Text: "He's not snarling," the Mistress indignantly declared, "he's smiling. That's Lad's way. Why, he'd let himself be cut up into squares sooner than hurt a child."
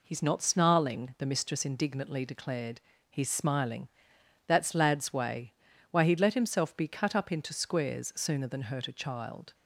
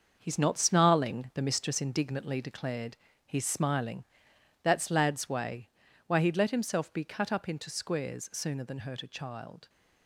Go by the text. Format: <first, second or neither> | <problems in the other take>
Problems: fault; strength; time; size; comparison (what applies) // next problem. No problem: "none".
first | gets quieter; strong; throughout; 7.5 dB